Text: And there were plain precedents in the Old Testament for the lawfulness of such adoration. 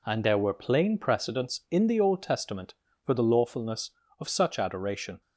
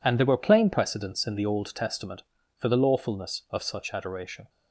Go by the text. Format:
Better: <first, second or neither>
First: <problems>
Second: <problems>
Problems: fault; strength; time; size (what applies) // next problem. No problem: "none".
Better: first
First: none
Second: gets quieter; strong; throughout; 10.5 dB